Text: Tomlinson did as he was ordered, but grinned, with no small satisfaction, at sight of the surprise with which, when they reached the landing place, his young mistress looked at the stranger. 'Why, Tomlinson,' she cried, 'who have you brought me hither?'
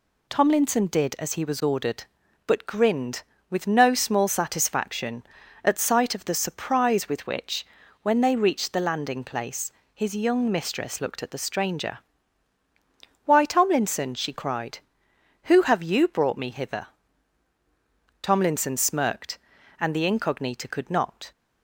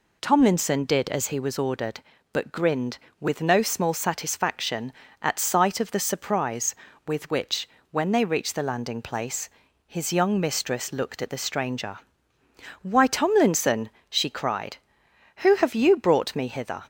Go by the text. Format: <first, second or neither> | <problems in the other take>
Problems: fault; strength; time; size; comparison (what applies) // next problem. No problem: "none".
second | goes on to say "Tomlinson smirked and the Incognita could not"; strong; from 18.2 s on; 3.1 s long